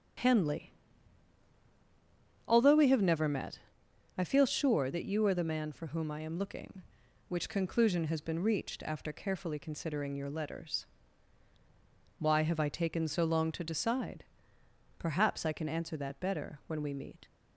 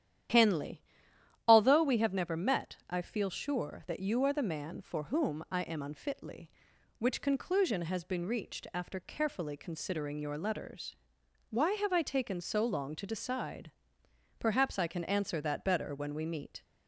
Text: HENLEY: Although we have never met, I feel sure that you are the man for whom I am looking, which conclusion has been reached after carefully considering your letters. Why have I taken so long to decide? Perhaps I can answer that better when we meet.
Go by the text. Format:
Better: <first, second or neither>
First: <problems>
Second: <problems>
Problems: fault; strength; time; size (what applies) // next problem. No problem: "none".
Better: first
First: starts louder than the rest; strong; until 2.9 s; 8.5 dB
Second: starts louder than the rest; strong; until 1.9 s; 11 dB // says "unfitly" for "looking"; at 5.8 s